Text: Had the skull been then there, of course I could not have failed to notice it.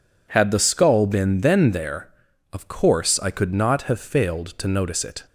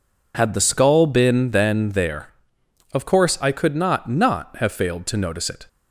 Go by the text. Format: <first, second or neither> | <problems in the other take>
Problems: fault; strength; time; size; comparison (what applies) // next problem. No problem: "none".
first | says "not" twice; at 4.0 s